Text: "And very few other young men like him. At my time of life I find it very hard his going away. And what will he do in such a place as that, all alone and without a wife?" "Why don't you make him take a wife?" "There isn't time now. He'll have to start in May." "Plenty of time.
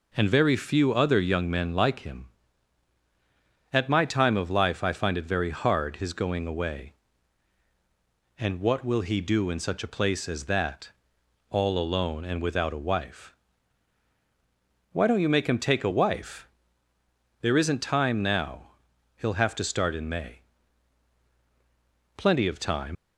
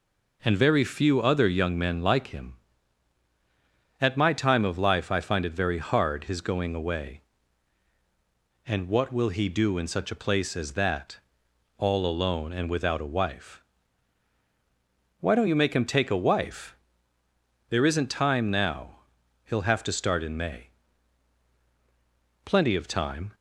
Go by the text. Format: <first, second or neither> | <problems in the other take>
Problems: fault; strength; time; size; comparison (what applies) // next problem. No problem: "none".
second | leaves "time" unfinished; at 22.9 s; 110 ms